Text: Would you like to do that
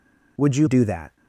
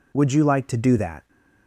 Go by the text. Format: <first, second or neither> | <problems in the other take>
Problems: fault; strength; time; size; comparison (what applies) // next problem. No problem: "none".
second | skips "like to"; at 0.6 s